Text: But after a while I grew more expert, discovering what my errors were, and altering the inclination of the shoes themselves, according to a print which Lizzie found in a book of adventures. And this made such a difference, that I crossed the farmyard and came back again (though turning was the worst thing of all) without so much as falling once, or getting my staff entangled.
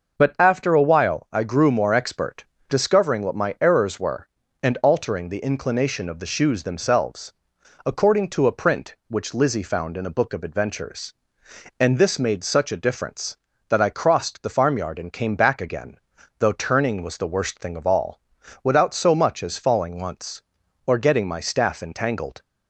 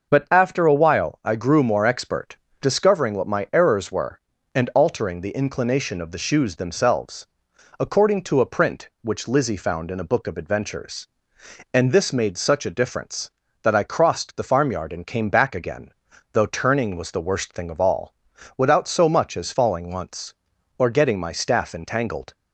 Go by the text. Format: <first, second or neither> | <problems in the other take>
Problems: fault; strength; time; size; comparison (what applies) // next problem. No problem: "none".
neither | none